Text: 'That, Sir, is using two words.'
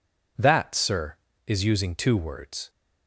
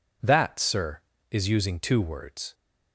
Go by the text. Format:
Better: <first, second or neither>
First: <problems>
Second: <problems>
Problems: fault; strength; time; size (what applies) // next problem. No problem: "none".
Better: neither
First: none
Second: none